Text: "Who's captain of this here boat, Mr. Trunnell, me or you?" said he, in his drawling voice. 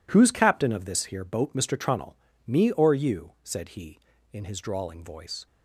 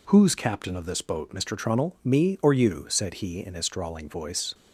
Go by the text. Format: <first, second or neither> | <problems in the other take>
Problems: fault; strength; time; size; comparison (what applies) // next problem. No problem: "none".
first | skips "here"; at 1.0 s